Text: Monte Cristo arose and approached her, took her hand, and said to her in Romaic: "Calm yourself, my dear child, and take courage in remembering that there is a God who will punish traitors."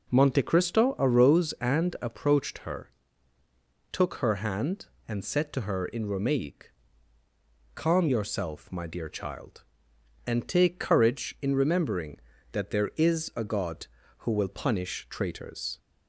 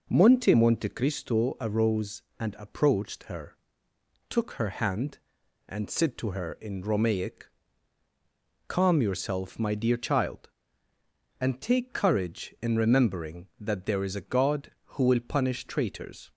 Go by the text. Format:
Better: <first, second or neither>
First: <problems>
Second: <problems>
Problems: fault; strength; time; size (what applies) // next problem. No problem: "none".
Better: first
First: none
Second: says "Monte" twice; at 0.5 s